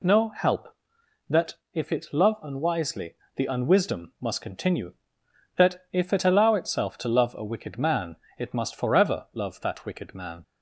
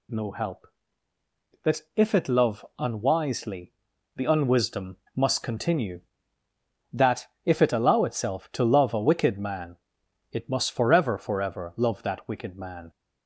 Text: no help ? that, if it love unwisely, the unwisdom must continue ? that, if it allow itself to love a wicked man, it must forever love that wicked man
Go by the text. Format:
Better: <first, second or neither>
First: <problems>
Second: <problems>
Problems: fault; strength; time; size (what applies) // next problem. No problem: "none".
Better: first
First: none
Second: pauses between "unwisdom" and "must"; slight; at 4.9 s; 0.18 s long // says "forever" twice; at 11.1 s